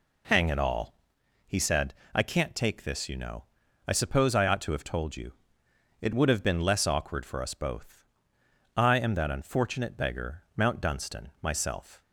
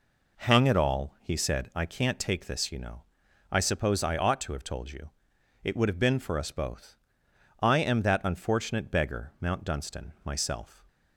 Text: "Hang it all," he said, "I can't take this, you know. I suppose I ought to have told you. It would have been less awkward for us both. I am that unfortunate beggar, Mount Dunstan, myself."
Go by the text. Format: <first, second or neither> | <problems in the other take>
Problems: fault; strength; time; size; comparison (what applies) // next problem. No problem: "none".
first | skips "less awkward"; at 6.1 s